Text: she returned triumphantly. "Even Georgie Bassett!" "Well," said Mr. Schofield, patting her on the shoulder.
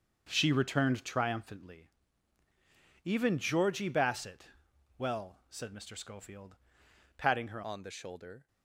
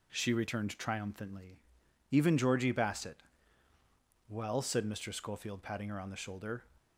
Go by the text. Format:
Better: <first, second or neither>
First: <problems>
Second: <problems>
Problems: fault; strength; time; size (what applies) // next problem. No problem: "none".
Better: second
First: starts louder than the rest; until 1.2 s; 6.5 dB // changes voice at "on"; from 7.6 s on; 0.8 s long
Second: none